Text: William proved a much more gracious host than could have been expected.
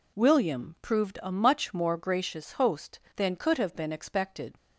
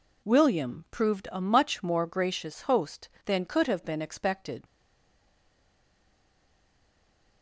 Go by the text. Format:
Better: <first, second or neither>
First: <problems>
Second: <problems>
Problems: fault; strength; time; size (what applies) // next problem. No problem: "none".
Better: first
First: none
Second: stays silent after the last word; strong; from 4.6 s on; 2.8 s long